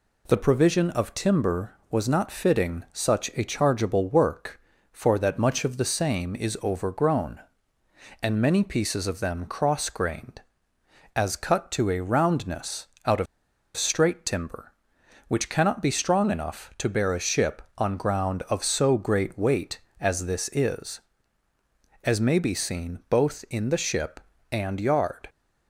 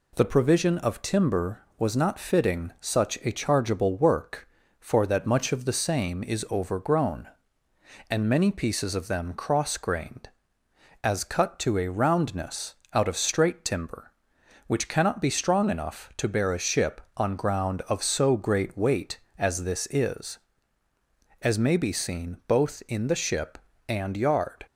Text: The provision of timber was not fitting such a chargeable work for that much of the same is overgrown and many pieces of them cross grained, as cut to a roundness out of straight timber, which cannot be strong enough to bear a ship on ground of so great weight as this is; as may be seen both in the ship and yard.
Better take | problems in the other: second | pauses between "roundness" and "out"; slight; at 12.8 s; 0.18 s long; slight in the second // pauses between "of" and "straight"; noticeable; at 13.2 s; 0.50 s long

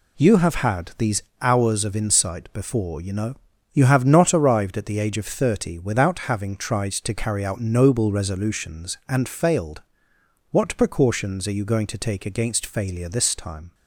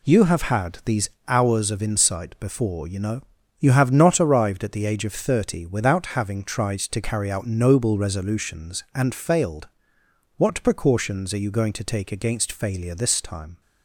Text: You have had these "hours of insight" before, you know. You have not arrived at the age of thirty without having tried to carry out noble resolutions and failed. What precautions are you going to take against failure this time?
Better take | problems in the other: neither | pauses between "these" and "hours"; slight; the same in both

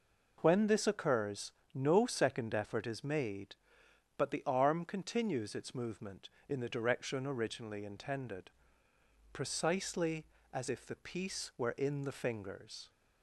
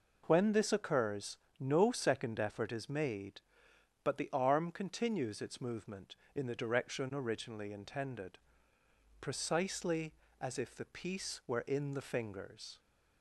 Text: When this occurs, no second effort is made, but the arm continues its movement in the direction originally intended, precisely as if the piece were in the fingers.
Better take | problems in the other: neither | none

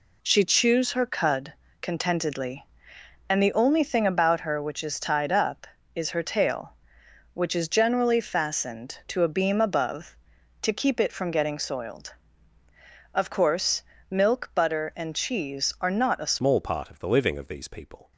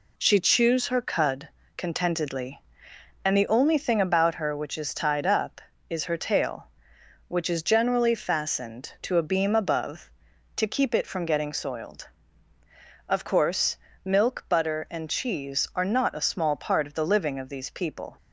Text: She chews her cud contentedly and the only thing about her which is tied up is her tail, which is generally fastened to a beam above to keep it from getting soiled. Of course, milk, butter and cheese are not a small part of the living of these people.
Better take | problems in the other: second | pauses between "cud" and "contentedly"; slight; at 1.5 s; 0.26 s long; slight in the second // changes voice at "small"; from 16.3 s on; 1.8 s long

